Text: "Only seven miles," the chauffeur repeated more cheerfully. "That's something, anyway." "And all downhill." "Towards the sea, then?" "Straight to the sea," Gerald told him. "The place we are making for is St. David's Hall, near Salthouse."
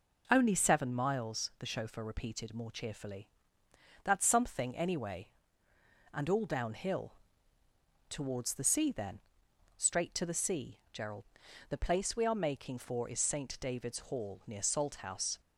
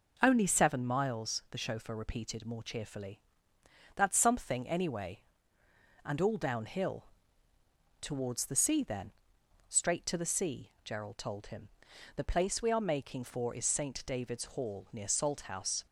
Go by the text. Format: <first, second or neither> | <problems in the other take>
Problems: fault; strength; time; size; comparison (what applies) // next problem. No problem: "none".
second | skips "told him"; at 11.4 s